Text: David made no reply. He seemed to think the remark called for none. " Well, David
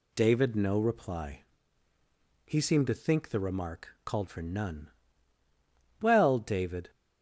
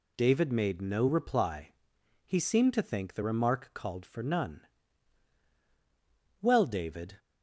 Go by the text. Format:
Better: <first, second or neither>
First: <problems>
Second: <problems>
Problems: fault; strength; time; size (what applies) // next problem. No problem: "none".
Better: second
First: skips "made"; at 0.5 s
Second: none